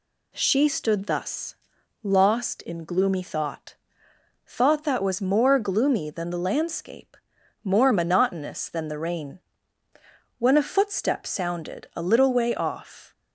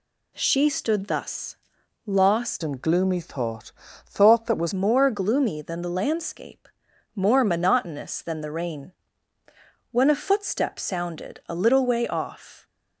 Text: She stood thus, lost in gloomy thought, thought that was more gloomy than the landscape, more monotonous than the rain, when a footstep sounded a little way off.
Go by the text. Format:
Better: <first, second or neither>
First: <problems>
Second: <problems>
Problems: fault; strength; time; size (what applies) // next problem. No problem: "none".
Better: first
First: none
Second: changes voice from "in" to "was"; from 2.6 to 4.7 s; 2.1 s long